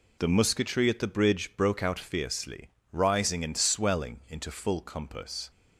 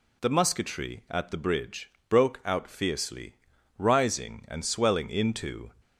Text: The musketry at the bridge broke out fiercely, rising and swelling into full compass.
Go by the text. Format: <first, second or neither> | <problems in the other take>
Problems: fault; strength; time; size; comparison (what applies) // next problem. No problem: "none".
first | pauses between "bridge" and "broke"; slight; at 1.9 s; 0.18 s long // stops before "full compass"; at 5.8 s